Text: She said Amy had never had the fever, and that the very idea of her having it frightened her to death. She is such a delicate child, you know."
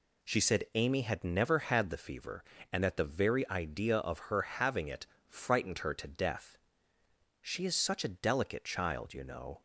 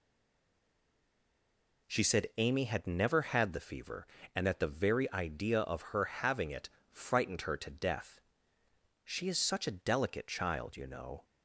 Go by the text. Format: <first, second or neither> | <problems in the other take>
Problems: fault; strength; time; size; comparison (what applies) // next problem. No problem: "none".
first | stays silent before the first word; noticeable; until 1.8 s; 1.8 s long // pauses between "it" and "frightened"; slight; at 6.6 s; 0.20 s long; slight in the first